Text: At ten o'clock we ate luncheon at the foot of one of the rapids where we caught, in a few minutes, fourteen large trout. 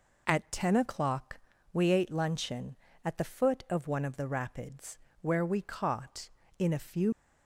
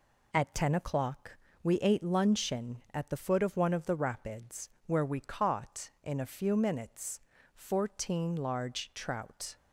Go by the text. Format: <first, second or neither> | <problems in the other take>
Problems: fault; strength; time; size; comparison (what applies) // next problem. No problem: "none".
second | pauses between "o'clock" and "we"; slight; at 1.3 s; 0.34 s long; slight in the second // pauses between "rapids" and "where"; slight; at 4.9 s; 0.24 s long; slight in the second // stops before "minutes fourteen large trout"; at 7.1 s